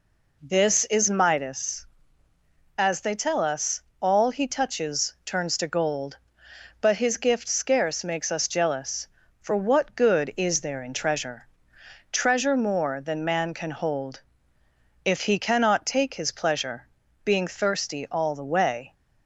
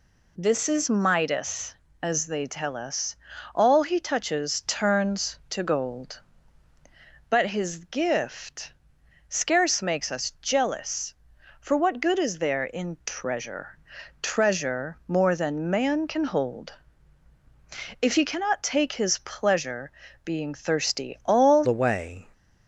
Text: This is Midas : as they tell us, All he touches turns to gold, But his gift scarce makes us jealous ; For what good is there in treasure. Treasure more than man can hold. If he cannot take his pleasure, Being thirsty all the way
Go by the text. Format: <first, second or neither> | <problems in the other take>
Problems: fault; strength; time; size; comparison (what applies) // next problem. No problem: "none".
first | pauses between "gift" and "scarce"; noticeable; at 8.7 s; 0.56 s long // changes voice at "the"; from 21.6 s on; 0.6 s long